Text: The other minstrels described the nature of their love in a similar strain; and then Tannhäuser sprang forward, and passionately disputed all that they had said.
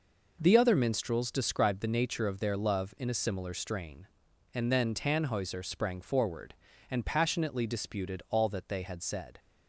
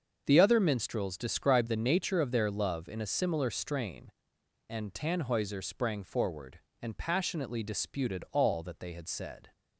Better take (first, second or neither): first